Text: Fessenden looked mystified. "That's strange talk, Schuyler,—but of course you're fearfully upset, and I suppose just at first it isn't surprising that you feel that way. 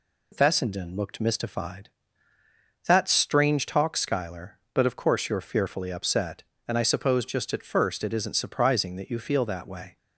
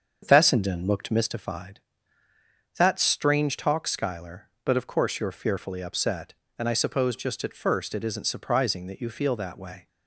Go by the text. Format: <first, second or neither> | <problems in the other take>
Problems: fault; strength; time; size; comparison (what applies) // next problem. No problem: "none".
first | starts louder than the rest; until 1.3 s; 7 dB